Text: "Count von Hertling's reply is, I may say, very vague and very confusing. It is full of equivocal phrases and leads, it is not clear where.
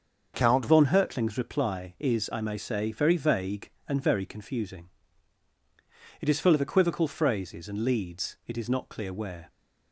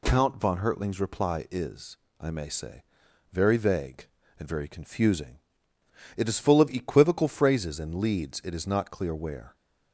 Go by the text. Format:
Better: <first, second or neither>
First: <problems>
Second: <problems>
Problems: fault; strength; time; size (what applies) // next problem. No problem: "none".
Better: second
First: starts louder than the rest; until 1.3 s; 6.5 dB // changes voice at "von"; from 0.6 s on; 8.9 s long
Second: none